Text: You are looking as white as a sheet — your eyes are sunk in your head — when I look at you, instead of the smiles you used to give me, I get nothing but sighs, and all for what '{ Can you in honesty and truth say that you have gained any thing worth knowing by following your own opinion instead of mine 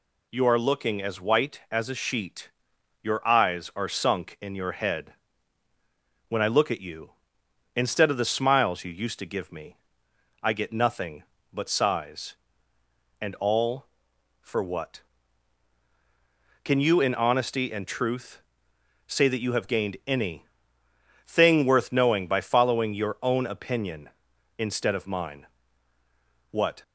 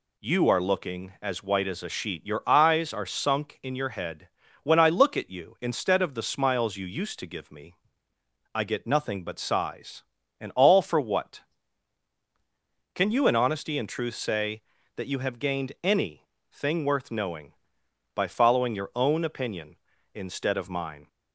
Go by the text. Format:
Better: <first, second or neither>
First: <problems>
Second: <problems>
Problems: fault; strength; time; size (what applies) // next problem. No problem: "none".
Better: second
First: pauses between "truth" and "say"; noticeable; at 18.4 s; 0.64 s long // pauses between "any" and "thing"; noticeable; at 20.4 s; 0.82 s long // goes on to say "What"; slight; from 26.5 s on; 0.32 s long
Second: pauses between "any" and "thing"; slight; at 16.2 s; 0.24 s long